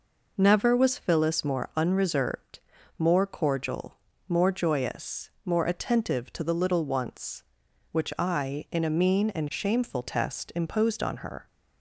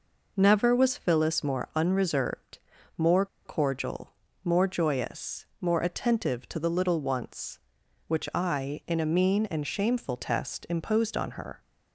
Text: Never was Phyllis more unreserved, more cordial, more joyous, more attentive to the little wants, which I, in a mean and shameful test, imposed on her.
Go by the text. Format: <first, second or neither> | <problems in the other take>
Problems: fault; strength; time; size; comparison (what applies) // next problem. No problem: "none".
first | pauses between "more" and "cordial"; slight; at 3.2 s; 0.19 s long